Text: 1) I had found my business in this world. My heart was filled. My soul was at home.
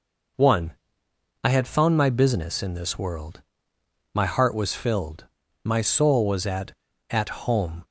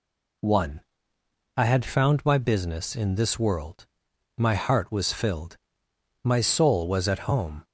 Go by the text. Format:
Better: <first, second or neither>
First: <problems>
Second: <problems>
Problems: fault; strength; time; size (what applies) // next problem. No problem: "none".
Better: second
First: says "at" twice; at 7.1 s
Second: none